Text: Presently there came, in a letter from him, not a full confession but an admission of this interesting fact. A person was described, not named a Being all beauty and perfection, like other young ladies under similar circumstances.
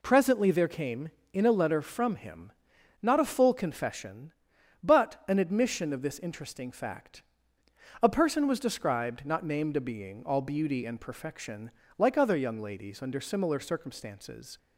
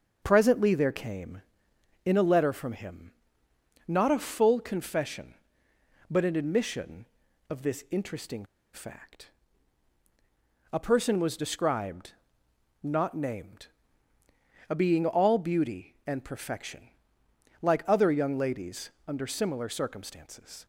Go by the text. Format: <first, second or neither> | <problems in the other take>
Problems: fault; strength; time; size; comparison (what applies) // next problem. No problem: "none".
first | starts louder than the rest; until 1.2 s; 6.5 dB // pauses between "interesting" and "fact"; slight; at 8.4 s; 0.29 s long // pauses between "named" and "a"; at 13.6 s; 1.0 s long // pauses between "ladies" and "under"; slight; at 18.8 s; 0.18 s long